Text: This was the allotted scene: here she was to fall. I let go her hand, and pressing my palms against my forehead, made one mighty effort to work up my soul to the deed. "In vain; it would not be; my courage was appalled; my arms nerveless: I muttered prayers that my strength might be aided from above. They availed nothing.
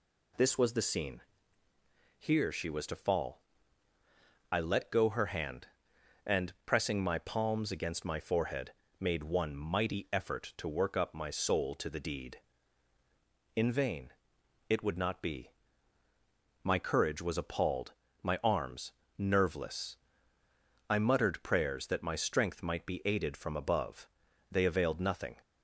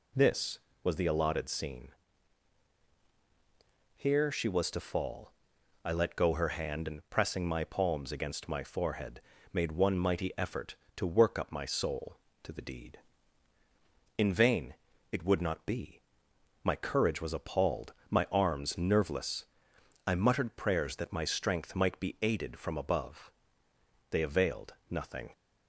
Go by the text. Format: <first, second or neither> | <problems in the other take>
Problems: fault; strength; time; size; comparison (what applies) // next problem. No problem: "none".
second | skips "allotted"; at 0.8 s // pauses between "arms" and "nerveless"; slight; at 18.9 s; 0.26 s long